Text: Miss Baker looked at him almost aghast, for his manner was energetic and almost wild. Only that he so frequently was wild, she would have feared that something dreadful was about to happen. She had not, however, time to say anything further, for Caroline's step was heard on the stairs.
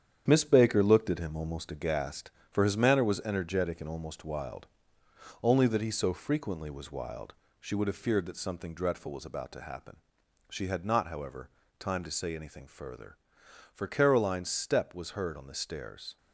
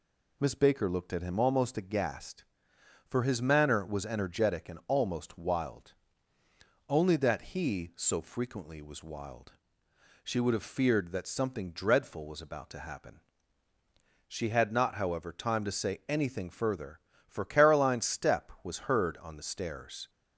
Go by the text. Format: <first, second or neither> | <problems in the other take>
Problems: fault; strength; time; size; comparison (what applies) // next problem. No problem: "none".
second | gets quieter; throughout; 6.5 dB